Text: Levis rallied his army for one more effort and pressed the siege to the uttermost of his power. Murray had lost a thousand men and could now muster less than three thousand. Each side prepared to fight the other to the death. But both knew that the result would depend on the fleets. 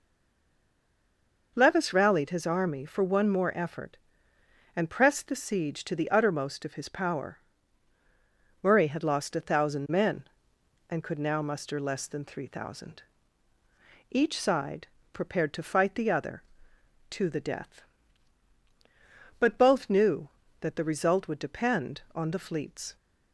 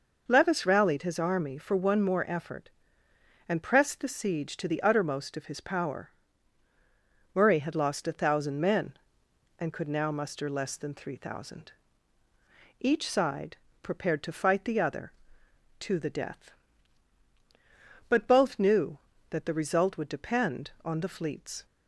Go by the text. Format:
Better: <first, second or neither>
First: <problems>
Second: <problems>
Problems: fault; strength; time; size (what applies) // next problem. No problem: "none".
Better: second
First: stays silent before the first word; noticeable; until 1.5 s; 1.5 s long // pauses between "side" and "prepared"; slight; at 14.8 s; 0.24 s long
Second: pauses between "side" and "prepared"; slight; at 13.5 s; 0.24 s long